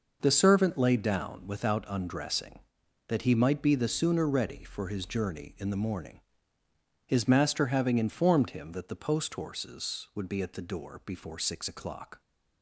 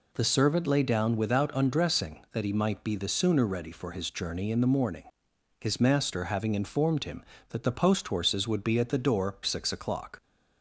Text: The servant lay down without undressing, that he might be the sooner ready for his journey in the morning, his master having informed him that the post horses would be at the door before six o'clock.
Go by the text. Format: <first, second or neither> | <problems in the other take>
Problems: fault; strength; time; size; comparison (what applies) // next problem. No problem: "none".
first | skips "before"; at 9.4 s